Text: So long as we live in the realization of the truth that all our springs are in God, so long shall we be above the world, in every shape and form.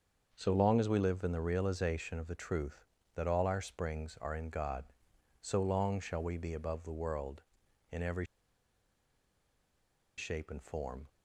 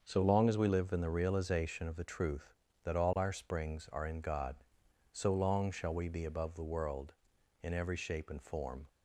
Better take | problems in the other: second | starts louder than the rest; until 1.3 s; 6.5 dB; also in the second // pauses between "every" and "shape"; strong; at 8.2 s; 1.9 s long

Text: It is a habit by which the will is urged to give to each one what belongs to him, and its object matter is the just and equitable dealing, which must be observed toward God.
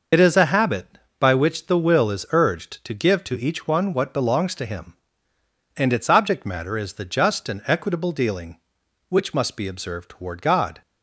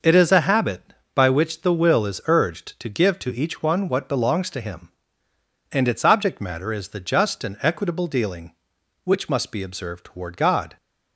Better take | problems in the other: second | loses the start of "It"; at 0.1 s; 55 ms

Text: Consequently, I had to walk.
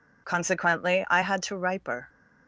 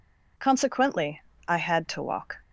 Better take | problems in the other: second | says "riper" for "walk"; at 1.5 s

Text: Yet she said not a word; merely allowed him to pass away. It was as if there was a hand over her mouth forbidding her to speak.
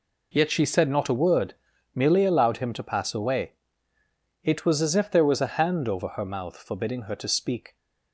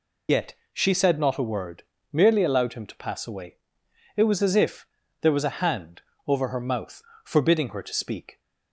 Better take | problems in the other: first | loses the start of "Yet"; at 0.2 s; 65 ms // pauses between "Yet" and "she"; slight; at 0.5 s; 0.18 s long // pauses between "if" and "there"; slight; at 4.8 s; 0.34 s long // pauses between "hand" and "over"; slight; at 6.0 s; 0.28 s long // pauses between "mouth" and "forbidding"; slight; at 7.0 s; 0.22 s long

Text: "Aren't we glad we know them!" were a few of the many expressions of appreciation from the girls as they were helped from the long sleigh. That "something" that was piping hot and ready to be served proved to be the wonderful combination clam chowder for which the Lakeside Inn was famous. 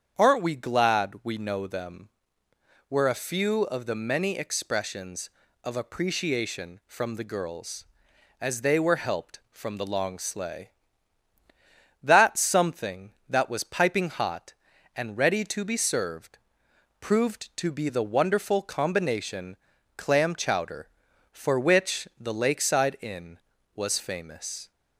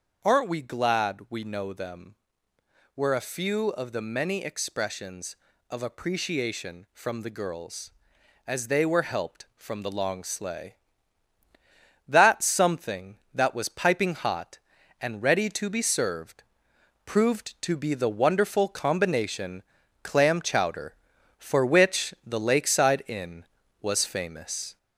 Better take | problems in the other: first | gets louder; slight; throughout; 3 dB // starts louder than the rest; until 1.3 s; 6.5 dB; strong in the first // pauses between "served" and "proved"; noticeable; at 16.4 s; 0.64 s long; noticeable in the first // pauses between "combination" and "clam"; at 19.6 s; 0.40 s long; also in the first

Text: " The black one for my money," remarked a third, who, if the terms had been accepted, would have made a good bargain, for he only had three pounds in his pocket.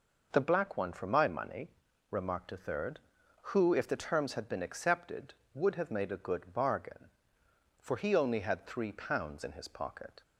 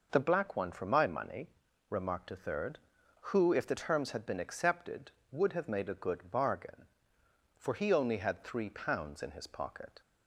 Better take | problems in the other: neither | none

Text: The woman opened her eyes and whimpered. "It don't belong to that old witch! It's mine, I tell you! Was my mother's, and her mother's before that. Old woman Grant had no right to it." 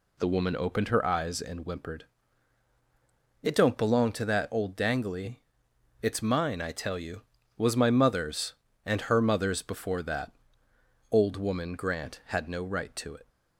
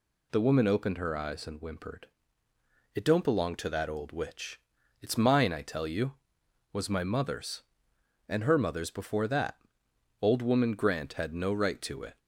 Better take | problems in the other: second | says "dangly" for "witch"; at 4.7 s

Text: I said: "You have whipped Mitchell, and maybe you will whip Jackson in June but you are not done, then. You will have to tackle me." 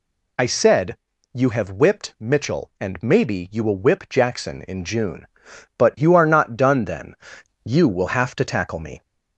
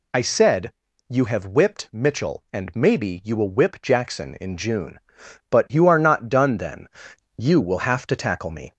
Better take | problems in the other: neither | none

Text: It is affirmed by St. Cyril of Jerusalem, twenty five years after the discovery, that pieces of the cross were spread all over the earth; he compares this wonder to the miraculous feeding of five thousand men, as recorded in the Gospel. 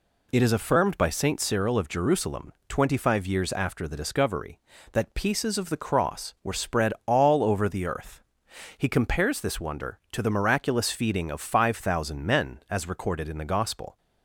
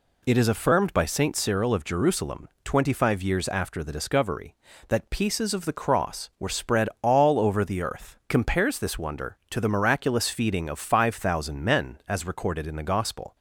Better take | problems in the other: first | skips "he"; at 8.2 s

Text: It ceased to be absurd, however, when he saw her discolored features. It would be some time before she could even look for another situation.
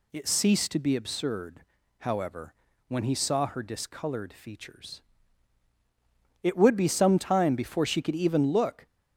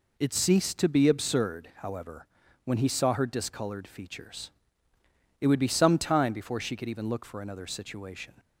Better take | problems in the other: second | stops before "for another situation"; at 8.8 s

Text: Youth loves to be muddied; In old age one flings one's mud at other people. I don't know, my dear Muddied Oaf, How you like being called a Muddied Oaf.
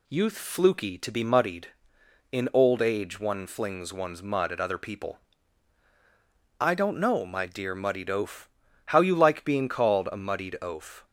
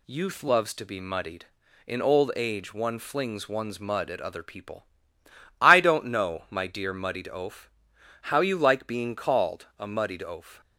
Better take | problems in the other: second | says "fluky" for "loves"; at 0.3 s

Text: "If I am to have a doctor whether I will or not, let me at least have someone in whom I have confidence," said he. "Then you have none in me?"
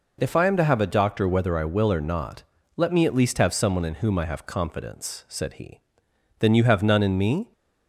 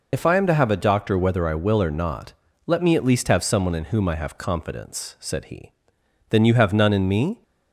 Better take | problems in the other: first | loses the start of "If"; at 0.1 s; 45 ms

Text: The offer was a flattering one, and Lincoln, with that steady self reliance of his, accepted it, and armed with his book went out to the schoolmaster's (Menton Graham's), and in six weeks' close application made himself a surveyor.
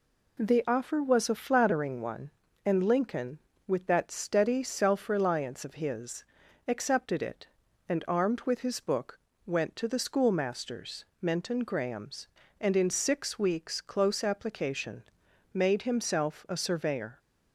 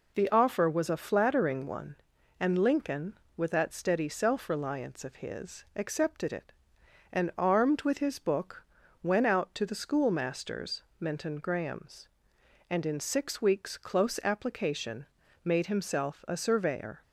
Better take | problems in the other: second | pauses between "book" and "went"; slight; at 9.1 s; 0.28 s long; also in the second // skips "out"; at 9.7 s // pauses between "application" and "made"; noticeable; at 15.0 s; 0.50 s long; also in the second

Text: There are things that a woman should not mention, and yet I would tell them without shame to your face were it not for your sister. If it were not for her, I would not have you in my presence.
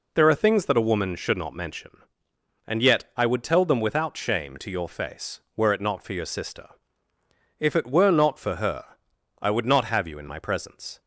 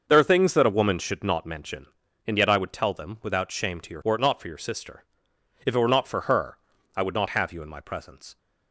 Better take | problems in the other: first | starts louder than the rest; until 1.1 s; 6 dB // skips "face"; at 4.0 s

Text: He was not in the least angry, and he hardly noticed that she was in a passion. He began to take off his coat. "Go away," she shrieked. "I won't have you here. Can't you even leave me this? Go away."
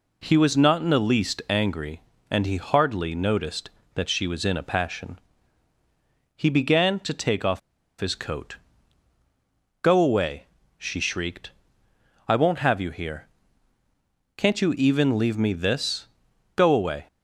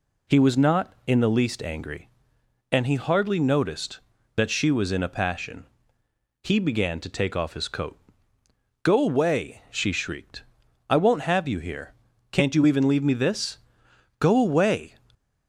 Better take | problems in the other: second | pauses between "off" and "his"; at 7.5 s; 0.40 s long

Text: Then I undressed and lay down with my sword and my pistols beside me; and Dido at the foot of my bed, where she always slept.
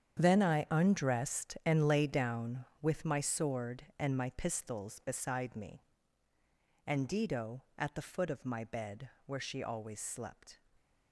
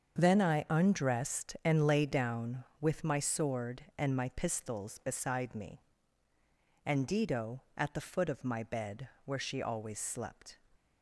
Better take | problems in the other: second | gets quieter; strong; throughout; 13.5 dB // starts louder than the rest; strong; until 1.2 s; 8.5 dB; also in the second

